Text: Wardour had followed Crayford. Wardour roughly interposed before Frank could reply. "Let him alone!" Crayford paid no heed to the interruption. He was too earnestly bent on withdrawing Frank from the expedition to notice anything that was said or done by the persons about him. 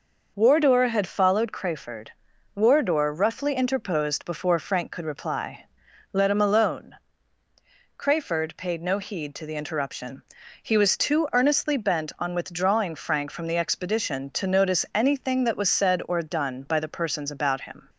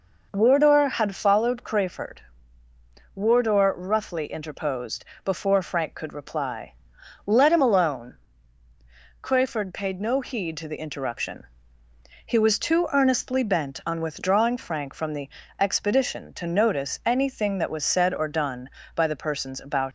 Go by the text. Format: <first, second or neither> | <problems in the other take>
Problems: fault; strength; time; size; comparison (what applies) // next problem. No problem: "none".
first | pauses between "interposed" and "before"; slight; at 5.0 s; 0.20 s long // pauses between "the" and "expedition"; slight; at 15.3 s; 0.28 s long // stops before "him"; at 19.8 s